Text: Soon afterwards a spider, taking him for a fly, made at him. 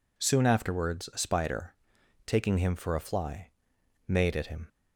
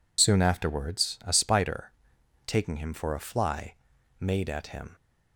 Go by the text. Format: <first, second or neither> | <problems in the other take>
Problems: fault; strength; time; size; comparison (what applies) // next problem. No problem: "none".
first | loses the start of "Soon"; at 0.1 s; 40 ms